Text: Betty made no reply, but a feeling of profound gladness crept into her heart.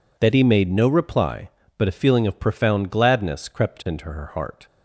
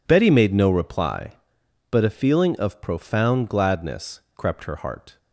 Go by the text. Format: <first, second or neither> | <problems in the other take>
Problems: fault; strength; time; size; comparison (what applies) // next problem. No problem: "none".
first | pauses between "gladness" and "crept"; slight; at 4.2 s; 0.16 s long // skips "into"; at 4.6 s